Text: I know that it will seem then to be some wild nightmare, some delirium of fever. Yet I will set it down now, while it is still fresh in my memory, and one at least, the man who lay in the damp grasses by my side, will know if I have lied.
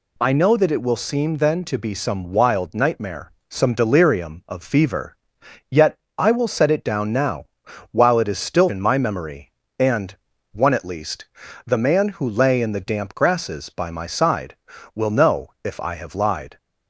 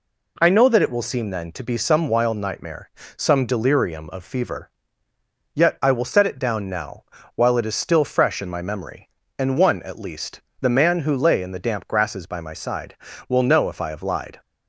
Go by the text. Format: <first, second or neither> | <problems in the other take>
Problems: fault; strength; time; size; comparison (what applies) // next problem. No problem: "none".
second | pauses between "Yet" and "I"; slight; at 5.9 s; 0.22 s long // skips "fresh"; at 8.7 s // pauses between "and" and "one"; slight; at 10.1 s; 0.34 s long